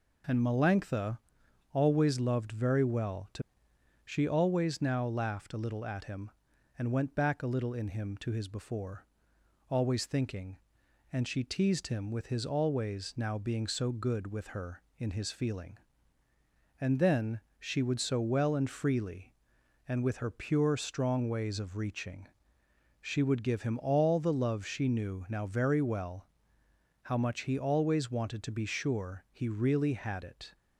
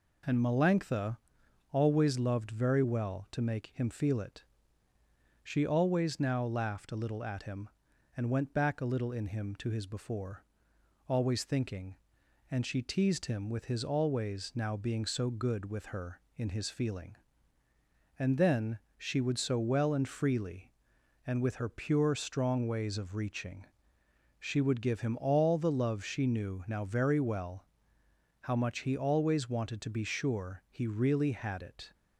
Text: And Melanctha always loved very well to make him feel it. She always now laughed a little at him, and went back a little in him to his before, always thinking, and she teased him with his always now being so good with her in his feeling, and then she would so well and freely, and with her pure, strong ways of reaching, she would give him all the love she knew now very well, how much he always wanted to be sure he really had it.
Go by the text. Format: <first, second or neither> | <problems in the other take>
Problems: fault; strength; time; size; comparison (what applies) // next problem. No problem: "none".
second | pauses between "Melanctha" and "always"; noticeable; at 1.1 s; 0.54 s long; noticeable in the second // skips "make him feel it"; at 3.7 s // pauses between "then" and "she"; slight; at 17.3 s; 0.20 s long; slight in the second